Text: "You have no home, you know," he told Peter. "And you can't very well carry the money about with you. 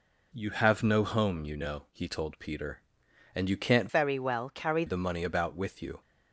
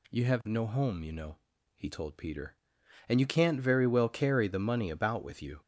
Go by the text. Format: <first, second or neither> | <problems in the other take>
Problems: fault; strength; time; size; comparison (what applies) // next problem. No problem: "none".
second | changes voice from "very" to "carry"; from 3.8 to 4.8 s; 1.0 s long